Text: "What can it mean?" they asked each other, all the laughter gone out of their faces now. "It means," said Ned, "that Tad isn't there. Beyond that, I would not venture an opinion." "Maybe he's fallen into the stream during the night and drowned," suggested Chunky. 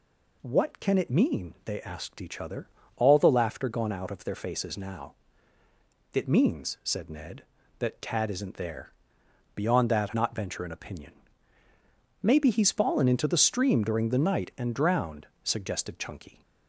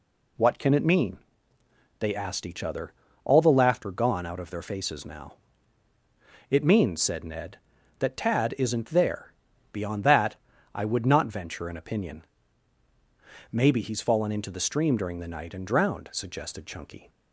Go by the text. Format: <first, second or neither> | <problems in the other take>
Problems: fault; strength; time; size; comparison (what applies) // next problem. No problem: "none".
second | skips "I would"; at 10.1 s